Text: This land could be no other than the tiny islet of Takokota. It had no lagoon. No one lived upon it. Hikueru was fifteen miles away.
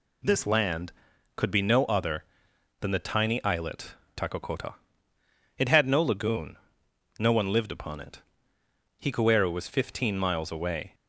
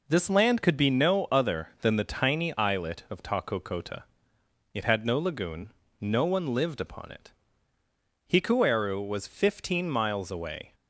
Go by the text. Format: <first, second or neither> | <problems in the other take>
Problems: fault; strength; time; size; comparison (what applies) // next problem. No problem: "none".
second | skips "of"; at 4.0 s